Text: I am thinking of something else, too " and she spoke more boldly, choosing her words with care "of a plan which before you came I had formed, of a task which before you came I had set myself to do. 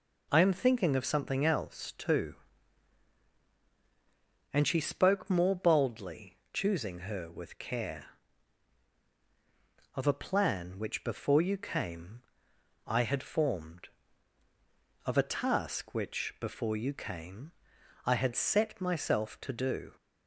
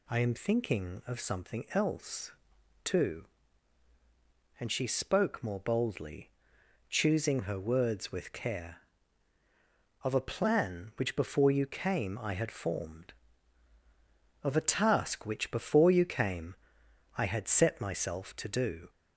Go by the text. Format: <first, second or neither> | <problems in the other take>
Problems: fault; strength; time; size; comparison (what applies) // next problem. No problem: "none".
second | skips "words"; at 7.2 s // pauses between "came" and "I"; noticeable; at 12.2 s; 0.64 s long // pauses between "came" and "I"; noticeable; at 17.5 s; 0.52 s long; noticeable in the second